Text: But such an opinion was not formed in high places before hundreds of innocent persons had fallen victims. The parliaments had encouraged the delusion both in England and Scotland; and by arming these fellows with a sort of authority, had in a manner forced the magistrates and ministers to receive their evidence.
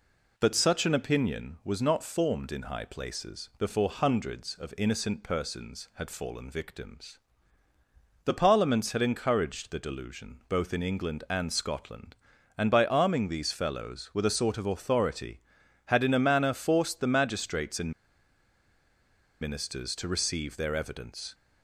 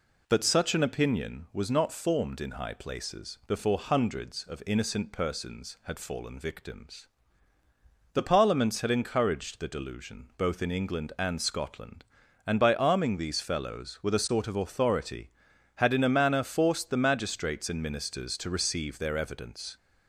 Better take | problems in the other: second | pauses between "and" and "ministers"; strong; at 17.9 s; 1.5 s long

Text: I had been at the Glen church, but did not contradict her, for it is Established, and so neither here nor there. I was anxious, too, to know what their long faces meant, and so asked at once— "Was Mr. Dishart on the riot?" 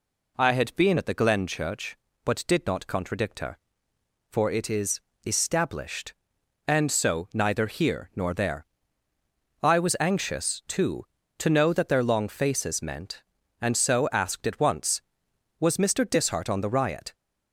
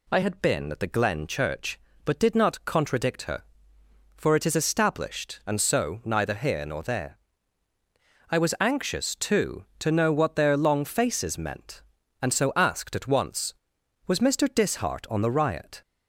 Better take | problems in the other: second | pauses between "is" and "Established"; slight; at 4.9 s; 0.24 s long // says "that" for "what"; at 11.7 s

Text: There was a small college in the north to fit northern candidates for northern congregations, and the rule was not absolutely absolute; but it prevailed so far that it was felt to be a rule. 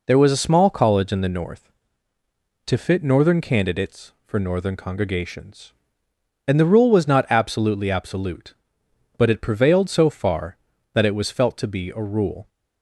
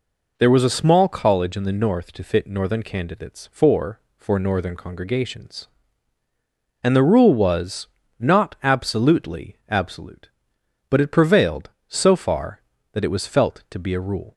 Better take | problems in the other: first | says "for" twice; at 4.1 s // pauses between "was" and "not"; slight; at 7.8 s; 0.32 s long

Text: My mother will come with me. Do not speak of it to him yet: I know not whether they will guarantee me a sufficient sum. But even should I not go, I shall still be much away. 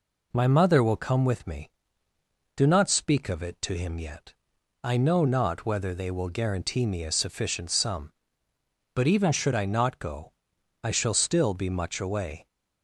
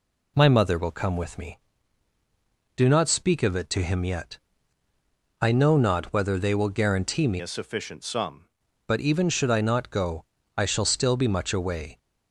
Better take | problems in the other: first | changes voice from "a" to "sum"; from 7.3 to 8.4 s; 1.1 s long

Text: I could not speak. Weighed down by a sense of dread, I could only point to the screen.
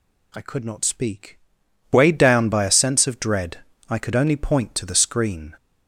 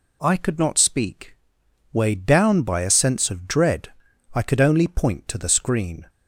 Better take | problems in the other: neither | none

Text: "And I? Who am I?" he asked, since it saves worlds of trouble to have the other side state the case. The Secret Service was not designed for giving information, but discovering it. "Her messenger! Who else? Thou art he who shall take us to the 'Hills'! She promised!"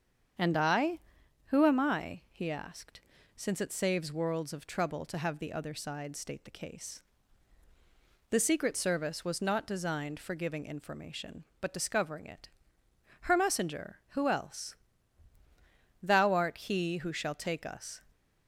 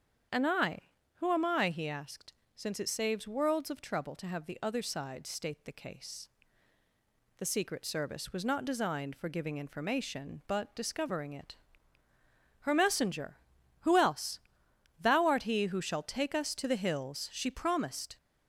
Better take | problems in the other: second | starts louder than the rest; strong; until 1.8 s; 7.5 dB; strong in the second // stops before "to the Hills She promised"; at 18.1 s

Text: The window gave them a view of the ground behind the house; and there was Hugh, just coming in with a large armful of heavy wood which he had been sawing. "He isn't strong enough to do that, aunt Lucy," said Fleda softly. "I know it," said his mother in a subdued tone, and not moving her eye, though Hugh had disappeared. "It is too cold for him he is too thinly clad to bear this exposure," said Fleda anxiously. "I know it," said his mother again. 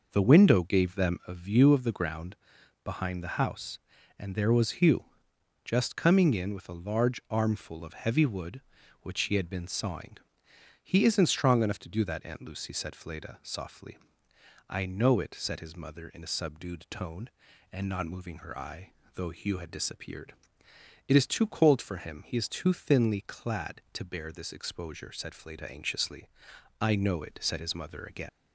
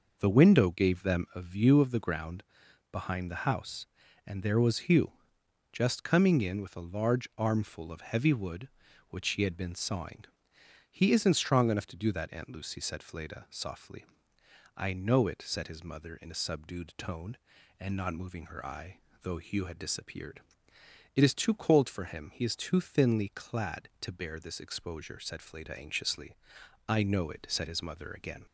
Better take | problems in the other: second | pauses between "ground" and "behind"; noticeable; at 2.3 s; 0.48 s long; noticeable in the second // leaves "again" unfinished; at 28.2 s; 90 ms

